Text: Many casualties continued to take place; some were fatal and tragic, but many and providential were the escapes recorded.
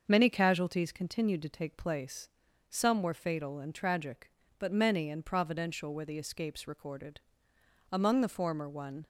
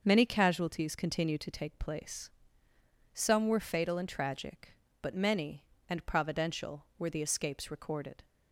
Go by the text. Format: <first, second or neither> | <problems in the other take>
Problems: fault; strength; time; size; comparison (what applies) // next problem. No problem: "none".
second | starts louder than the rest; until 1.0 s; 6.5 dB; also in the second // goes on to say "Among the former one"; noticeable; from 7.9 s on; 1.1 s long